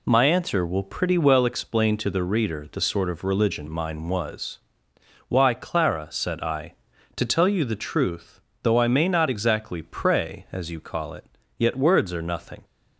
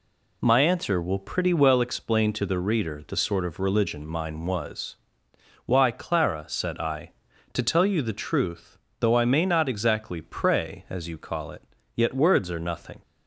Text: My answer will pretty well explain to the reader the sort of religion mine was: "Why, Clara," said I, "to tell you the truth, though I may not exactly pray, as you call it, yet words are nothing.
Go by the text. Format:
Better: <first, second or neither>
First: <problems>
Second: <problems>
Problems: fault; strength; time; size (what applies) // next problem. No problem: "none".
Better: neither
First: none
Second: none